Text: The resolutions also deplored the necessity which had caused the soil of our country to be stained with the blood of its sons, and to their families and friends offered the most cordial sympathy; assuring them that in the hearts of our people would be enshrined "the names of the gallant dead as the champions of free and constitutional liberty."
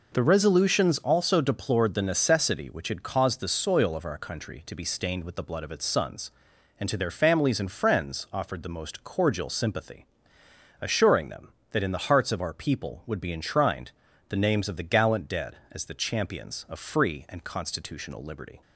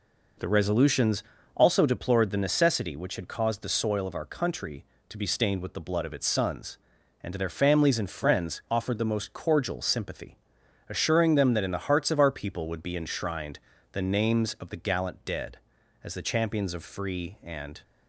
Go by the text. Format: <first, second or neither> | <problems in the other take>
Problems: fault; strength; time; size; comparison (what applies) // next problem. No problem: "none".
first | pauses between "resolutions" and "also"; slight; at 1.2 s; 0.32 s long // pauses between "enshrined" and "the"; slight; at 13.5 s; 0.32 s long; also in the first // stops before "constitutional liberty"; at 17.8 s